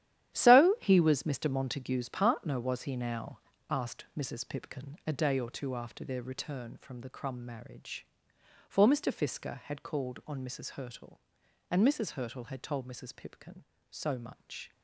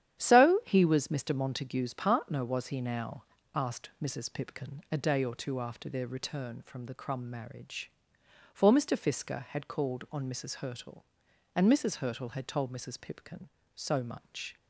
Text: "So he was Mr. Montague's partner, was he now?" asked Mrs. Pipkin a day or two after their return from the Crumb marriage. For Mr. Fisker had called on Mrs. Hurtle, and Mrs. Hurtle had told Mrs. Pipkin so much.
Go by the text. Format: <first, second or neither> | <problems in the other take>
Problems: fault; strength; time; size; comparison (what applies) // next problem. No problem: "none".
second | gets quieter; strong; throughout; 12 dB // starts louder than the rest; strong; until 1.3 s; 11.5 dB; strong in the second